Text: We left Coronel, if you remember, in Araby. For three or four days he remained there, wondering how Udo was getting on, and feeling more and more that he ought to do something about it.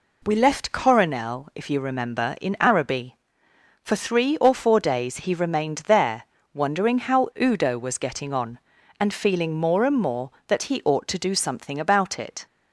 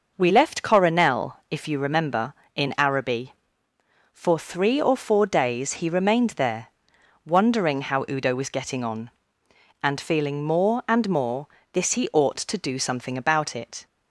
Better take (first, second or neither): first